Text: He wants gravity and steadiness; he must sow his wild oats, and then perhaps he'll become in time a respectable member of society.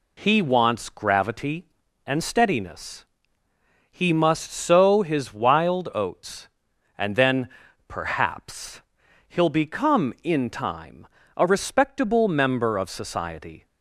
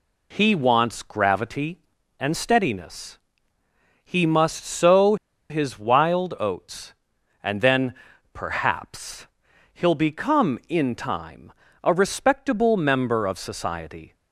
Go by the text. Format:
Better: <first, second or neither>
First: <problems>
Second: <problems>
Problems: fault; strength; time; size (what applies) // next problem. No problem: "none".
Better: first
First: pauses between "then" and "perhaps"; at 7.4 s; 0.38 s long // pauses between "perhaps" and "he'll"; noticeable; at 8.8 s; 0.48 s long // pauses between "time" and "a"; slight; at 11.0 s; 0.30 s long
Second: pauses between "sow" and "his"; slight; at 5.1 s; 0.34 s long // pauses between "then" and "perhaps"; at 7.9 s; 0.38 s long // pauses between "perhaps" and "he'll"; noticeable; at 9.2 s; 0.48 s long // pauses between "time" and "a"; slight; at 11.5 s; 0.32 s long